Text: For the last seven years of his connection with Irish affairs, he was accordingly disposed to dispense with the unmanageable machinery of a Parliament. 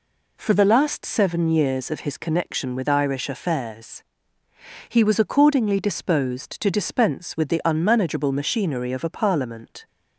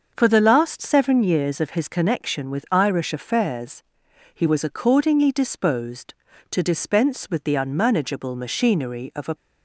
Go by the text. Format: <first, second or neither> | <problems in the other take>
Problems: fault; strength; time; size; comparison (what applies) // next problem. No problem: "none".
first | starts louder than the rest; until 1.1 s; 6.5 dB // stops before "Parliament"; at 9.3 s